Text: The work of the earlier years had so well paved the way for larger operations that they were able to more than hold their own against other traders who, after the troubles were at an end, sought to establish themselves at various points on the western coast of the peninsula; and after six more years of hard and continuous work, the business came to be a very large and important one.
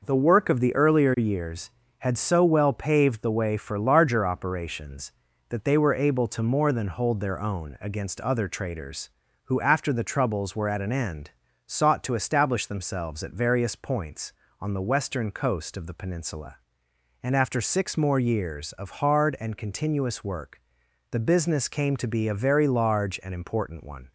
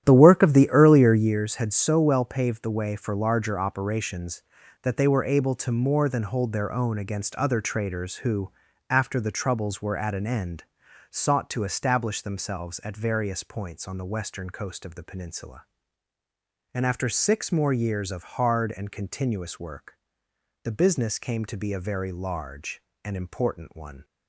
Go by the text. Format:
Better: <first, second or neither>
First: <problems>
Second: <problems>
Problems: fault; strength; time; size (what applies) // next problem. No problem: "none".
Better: first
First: none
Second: starts louder than the rest; strong; until 1.3 s; 11.5 dB